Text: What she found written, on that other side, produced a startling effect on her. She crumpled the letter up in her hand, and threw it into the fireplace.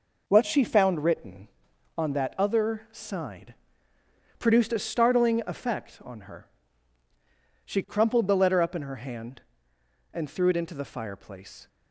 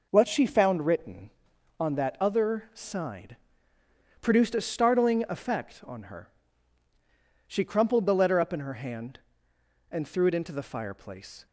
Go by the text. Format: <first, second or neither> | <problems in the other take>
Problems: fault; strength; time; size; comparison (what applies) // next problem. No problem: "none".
neither | none